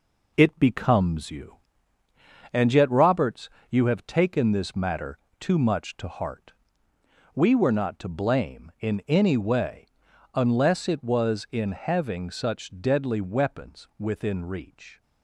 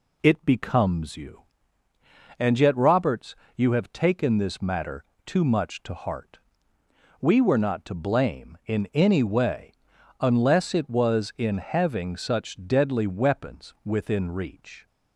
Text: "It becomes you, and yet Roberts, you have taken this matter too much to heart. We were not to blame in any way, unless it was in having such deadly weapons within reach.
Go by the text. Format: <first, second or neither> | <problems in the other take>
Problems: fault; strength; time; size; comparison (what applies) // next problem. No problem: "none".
second | gets quieter; noticeable; throughout; 5.5 dB // pauses between "matter" and "too"; slight; at 5.1 s; 0.22 s long; slight in the second